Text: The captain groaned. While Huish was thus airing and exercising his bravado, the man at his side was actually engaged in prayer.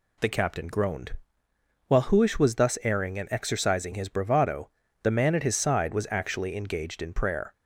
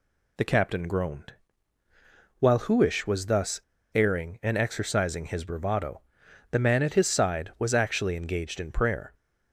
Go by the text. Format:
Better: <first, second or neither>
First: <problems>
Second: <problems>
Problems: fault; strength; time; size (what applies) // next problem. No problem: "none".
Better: first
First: none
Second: pauses between "thus" and "airing"; slight; at 3.5 s; 0.35 s long